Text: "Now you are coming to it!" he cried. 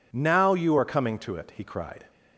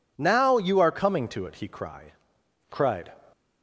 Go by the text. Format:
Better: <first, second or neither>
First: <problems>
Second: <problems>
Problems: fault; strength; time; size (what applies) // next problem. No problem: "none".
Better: first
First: none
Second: says "cried" twice; at 2.7 s